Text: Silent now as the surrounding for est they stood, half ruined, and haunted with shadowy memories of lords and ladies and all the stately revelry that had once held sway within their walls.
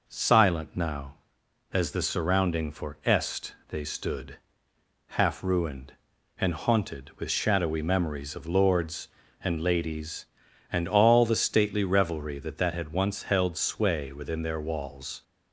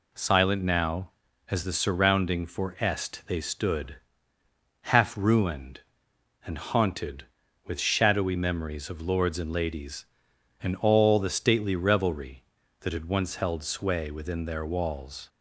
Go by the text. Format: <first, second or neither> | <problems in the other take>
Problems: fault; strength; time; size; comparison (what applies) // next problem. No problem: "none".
second | says "that" twice; at 12.5 s